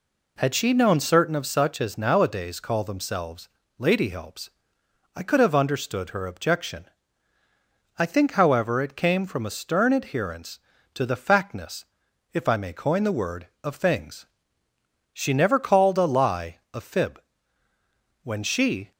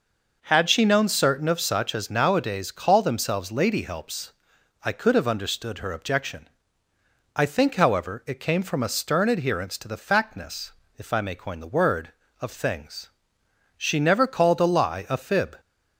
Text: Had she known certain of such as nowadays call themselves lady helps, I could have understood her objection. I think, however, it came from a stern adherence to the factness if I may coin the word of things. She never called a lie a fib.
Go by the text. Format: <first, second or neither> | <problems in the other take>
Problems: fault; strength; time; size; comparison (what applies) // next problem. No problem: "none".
second | pauses between "themselves" and "lady"; slight; at 3.4 s; 0.30 s long // pauses between "factness" and "if"; noticeable; at 11.8 s; 0.48 s long; slight in the second // goes on to say "When she"; noticeable; from 18.2 s on; 0.70 s long